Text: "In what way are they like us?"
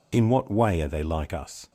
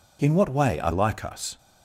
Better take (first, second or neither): first